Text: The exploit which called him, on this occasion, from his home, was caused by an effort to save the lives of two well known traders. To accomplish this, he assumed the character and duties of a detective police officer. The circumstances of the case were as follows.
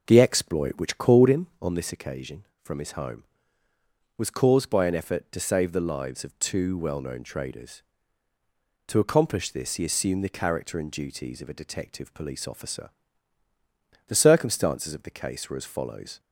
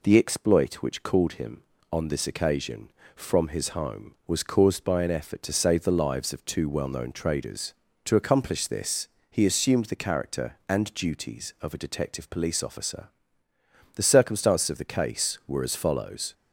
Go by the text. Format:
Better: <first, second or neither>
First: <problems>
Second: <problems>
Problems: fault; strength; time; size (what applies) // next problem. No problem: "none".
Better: second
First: starts louder than the rest; noticeable; until 1.9 s; 5.5 dB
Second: none